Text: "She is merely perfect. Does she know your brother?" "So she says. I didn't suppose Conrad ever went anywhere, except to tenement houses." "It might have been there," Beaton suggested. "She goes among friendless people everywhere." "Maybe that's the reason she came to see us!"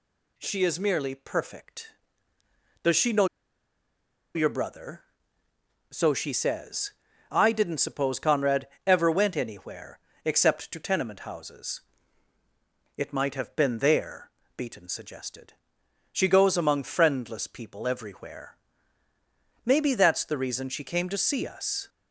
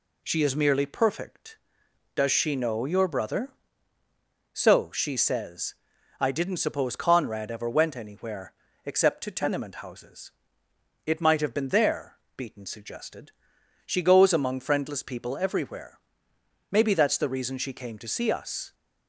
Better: second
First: pauses between "know" and "your"; at 3.2 s; 1.0 s long // pauses between "Conrad" and "ever"; slight; at 8.6 s; 0.18 s long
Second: none

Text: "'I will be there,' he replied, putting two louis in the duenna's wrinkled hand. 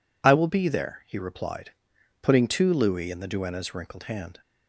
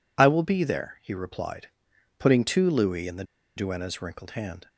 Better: first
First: none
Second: pauses between "the" and "duenna's"; slight; at 3.2 s; 0.32 s long

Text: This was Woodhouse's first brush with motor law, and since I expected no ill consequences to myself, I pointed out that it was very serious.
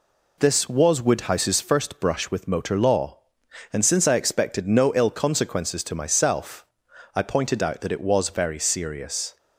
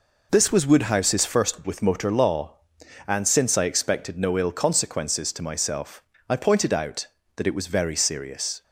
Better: first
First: none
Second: skips "brush"; at 1.6 s

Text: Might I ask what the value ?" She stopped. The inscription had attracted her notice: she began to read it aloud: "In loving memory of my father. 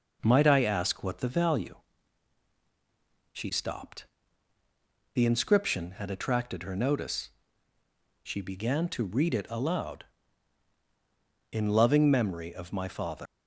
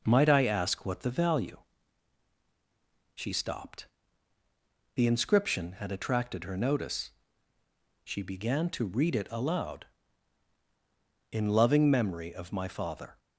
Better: second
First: leaves "father" unfinished; at 13.2 s; 135 ms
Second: none

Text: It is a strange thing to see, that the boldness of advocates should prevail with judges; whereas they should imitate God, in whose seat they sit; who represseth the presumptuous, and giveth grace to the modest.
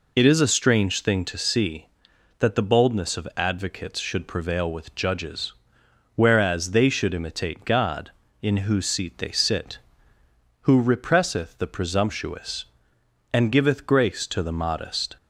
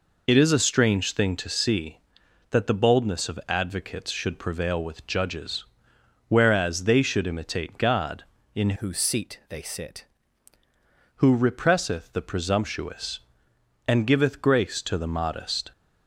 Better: first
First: none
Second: changes voice from "whose" to "sit"; from 8.7 to 10.0 s; 1.3 s long

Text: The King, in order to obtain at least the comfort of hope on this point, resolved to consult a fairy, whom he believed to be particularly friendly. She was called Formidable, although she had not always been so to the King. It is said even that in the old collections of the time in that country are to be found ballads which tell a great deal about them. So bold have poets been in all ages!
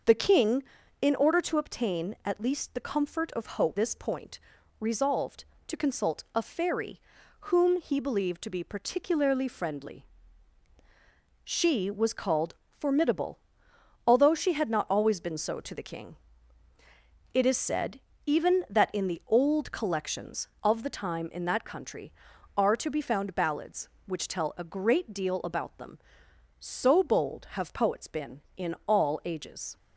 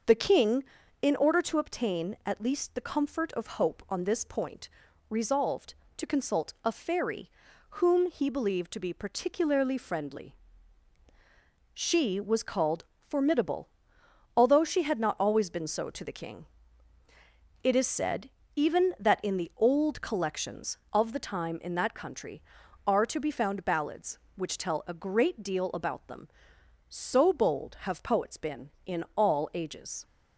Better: second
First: starts louder than the rest; noticeable; until 1.4 s; 6 dB // skips "on"; at 3.7 s // pauses between "called" and "Formidable"; slight; at 12.5 s; 0.24 s long // pauses between "said" and "even"; slight; at 17.9 s; 0.26 s long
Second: starts louder than the rest; noticeable; until 1.4 s; 6 dB // pauses between "called" and "Formidable"; slight; at 12.8 s; 0.24 s long // pauses between "said" and "even"; slight; at 18.2 s; 0.26 s long

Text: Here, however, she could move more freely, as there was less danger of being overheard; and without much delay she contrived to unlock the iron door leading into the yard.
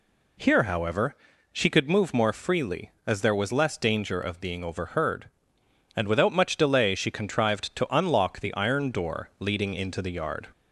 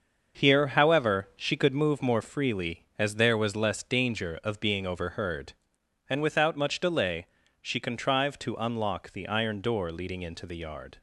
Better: first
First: none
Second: gets quieter; throughout; 7 dB // pauses between "delay" and "she"; slight; at 7.2 s; 0.36 s long

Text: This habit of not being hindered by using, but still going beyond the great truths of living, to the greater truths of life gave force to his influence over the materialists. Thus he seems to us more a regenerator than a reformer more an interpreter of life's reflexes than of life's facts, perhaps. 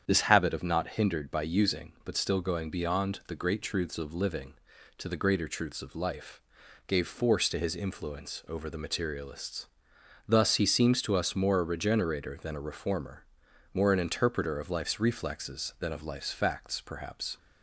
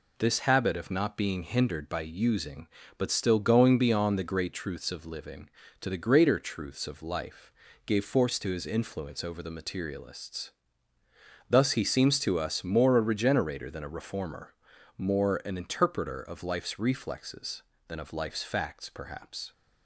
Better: second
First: starts louder than the rest; strong; until 1.0 s; 8.5 dB // skips "being"; at 0.8 s // pauses between "life" and "gave"; noticeable; at 6.4 s; 0.46 s long // pauses between "reformer" and "more"; noticeable; at 13.2 s; 0.50 s long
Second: pauses between "life" and "gave"; slight; at 7.5 s; 0.32 s long // pauses between "reformer" and "more"; noticeable; at 14.5 s; 0.46 s long

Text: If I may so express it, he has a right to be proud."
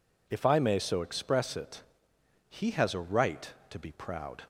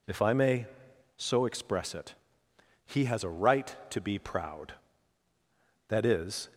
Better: first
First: none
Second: goes on to say "That is"; noticeable; from 5.8 s on; 0.62 s long

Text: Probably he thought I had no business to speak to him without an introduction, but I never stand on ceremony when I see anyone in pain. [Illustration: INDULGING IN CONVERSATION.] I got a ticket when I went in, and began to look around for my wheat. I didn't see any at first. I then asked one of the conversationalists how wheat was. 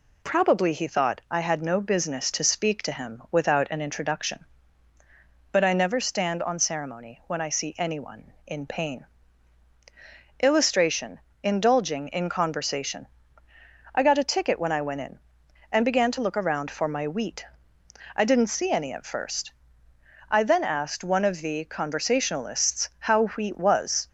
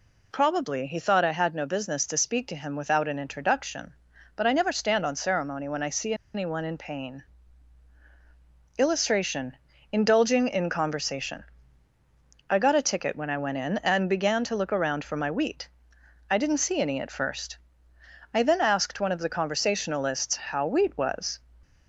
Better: first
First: none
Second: pauses between "see" and "anyone"; slight; at 6.1 s; 0.20 s long

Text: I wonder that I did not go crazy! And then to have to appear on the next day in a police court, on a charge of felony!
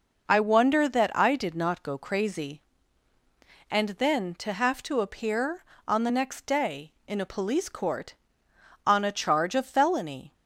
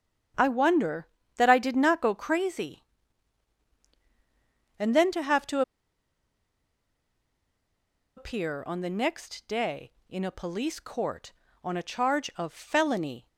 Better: first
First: none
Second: starts louder than the rest; strong; until 1.6 s; 8.5 dB // pauses between "to" and "appear"; strong; at 5.6 s; 2.5 s long

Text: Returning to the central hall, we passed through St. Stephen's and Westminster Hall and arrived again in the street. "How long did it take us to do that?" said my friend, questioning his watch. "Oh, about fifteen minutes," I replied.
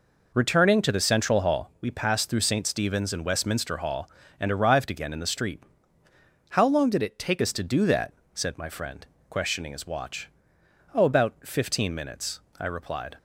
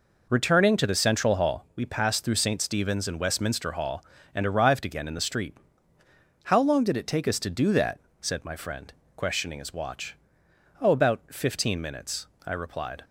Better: second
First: changes voice from "it" to "take"; from 7.0 to 7.4 s; 0.4 s long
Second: none

